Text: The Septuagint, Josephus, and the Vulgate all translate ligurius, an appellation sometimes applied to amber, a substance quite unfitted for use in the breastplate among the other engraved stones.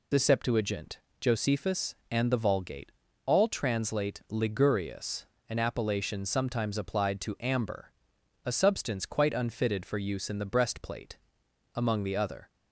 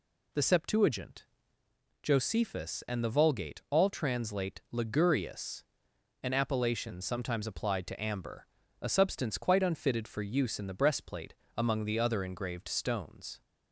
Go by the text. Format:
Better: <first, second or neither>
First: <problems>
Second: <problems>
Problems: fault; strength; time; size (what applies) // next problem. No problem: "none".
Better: second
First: pauses between "Vulgate" and "all"; slight; at 2.9 s; 0.32 s long // pauses between "breastplate" and "among"; noticeable; at 11.1 s; 0.60 s long // stops before "engraved stones"; at 12.5 s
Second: pauses between "breastplate" and "among"; slight; at 11.3 s; 0.23 s long